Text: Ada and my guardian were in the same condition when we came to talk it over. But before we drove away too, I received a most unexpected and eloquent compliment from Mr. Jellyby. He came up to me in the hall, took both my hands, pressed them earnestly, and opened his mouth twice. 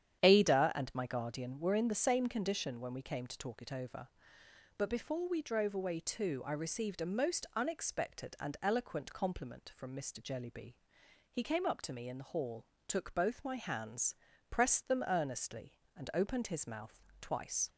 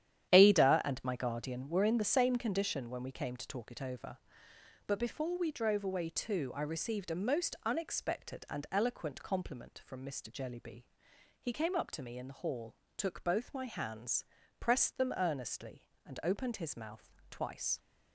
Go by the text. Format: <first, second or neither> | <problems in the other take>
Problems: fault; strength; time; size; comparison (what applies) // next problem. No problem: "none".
first | gets quieter; strong; throughout; 9 dB // starts louder than the rest; strong; until 1.3 s; 10.5 dB; strong in the first // pauses between "mouth" and "twice"; slight; at 17.0 s; 0.22 s long; slight in the first